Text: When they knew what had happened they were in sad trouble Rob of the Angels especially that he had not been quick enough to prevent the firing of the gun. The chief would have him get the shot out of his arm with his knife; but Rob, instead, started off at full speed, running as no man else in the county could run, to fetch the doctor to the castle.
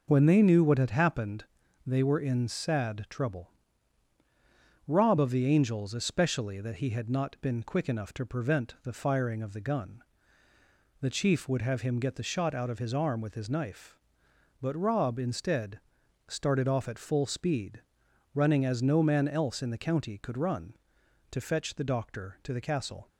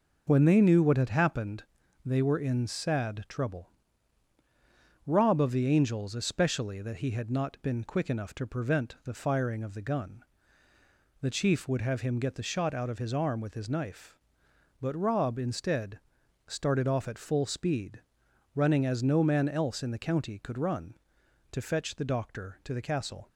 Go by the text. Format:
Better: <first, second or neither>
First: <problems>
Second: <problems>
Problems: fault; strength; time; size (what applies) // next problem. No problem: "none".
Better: neither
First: pauses between "happened" and "they"; at 1.4 s; 0.42 s long // pauses between "trouble" and "Rob"; strong; at 3.5 s; 1.3 s long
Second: pauses between "happened" and "they"; at 1.6 s; 0.42 s long // pauses between "trouble" and "Rob"; strong; at 3.6 s; 1.3 s long